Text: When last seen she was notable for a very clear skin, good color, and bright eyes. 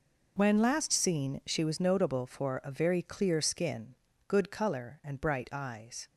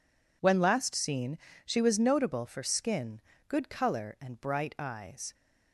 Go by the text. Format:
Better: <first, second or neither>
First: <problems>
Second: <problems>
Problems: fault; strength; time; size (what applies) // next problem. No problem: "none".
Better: first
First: none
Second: pauses between "seen" and "she"; slight; at 1.3 s; 0.28 s long // skips "a very clear"; at 2.6 s